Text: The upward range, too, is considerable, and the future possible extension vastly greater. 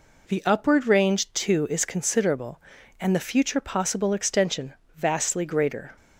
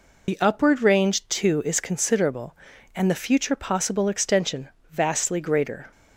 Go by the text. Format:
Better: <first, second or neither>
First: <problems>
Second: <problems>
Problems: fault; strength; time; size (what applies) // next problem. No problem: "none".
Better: first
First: pauses between "extension" and "vastly"; slight; at 4.7 s; 0.22 s long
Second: loses the start of "The"; at 0.2 s; 50 ms // pauses between "extension" and "vastly"; slight; at 4.6 s; 0.22 s long